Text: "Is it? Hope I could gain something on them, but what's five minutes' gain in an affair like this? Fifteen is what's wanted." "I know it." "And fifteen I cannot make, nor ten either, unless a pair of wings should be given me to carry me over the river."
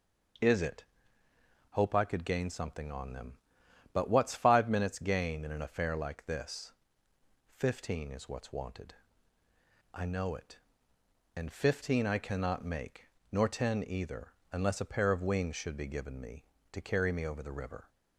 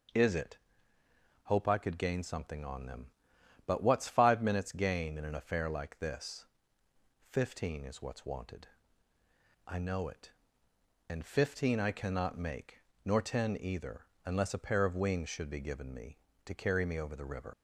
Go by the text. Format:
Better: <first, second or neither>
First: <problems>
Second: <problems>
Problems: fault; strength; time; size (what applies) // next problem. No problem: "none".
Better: first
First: starts louder than the rest; noticeable; until 2.2 s; 6 dB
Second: starts louder than the rest; noticeable; until 2.0 s; 6 dB // leaves "river" unfinished; at 17.5 s; 85 ms